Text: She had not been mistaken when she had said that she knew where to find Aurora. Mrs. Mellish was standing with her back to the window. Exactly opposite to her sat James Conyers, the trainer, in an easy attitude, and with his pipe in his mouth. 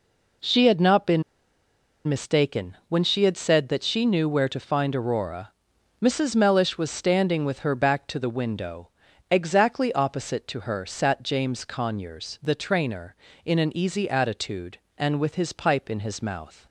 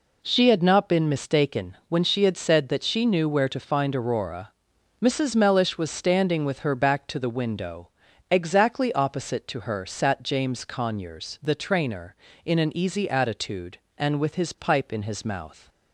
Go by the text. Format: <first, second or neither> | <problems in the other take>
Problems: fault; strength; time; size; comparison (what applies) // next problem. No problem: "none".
second | pauses between "been" and "mistaken"; noticeable; at 1.2 s; 0.85 s long